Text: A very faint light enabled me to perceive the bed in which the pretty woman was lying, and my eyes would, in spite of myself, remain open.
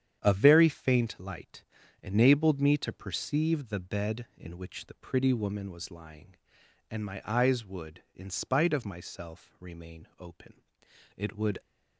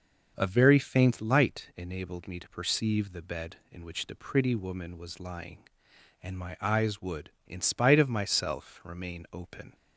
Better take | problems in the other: second | starts louder than the rest; strong; until 1.2 s; 9 dB // pauses between "light" and "enabled"; at 1.6 s; 0.38 s long // goes on to say "It would"; slight; from 11.1 s on; 0.44 s long

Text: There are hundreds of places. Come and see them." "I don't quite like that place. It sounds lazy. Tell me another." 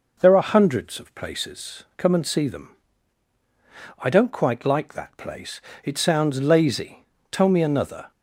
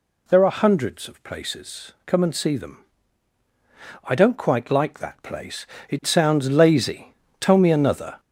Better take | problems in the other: first | gets louder; noticeable; throughout; 4.5 dB

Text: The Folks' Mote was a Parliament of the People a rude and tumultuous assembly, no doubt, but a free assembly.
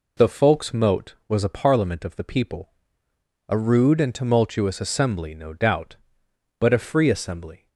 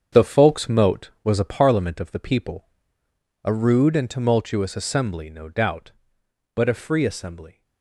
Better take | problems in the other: first | gets quieter; strong; throughout; 9.5 dB // pauses between "People" and "a"; noticeable; at 2.6 s; 0.76 s long; noticeable in the first

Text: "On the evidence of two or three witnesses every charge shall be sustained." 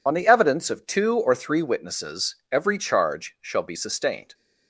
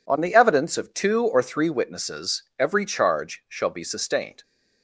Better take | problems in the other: second | loses the start of "On"; at 0.0 s; 30 ms // pauses between "witnesses" and "every"; slight; at 2.3 s; 0.16 s long; slight in the second

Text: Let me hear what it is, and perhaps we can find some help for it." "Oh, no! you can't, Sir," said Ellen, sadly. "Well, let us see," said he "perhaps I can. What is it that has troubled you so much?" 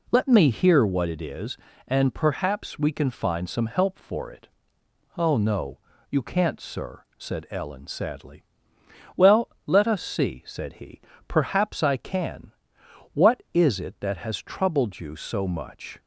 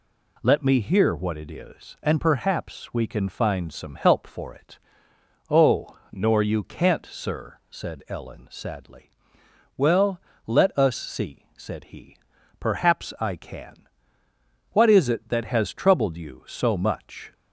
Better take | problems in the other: first | says "nor" for "no"; at 6.1 s // pauses between "he" and "perhaps"; at 12.1 s; 0.42 s long; slight in the first

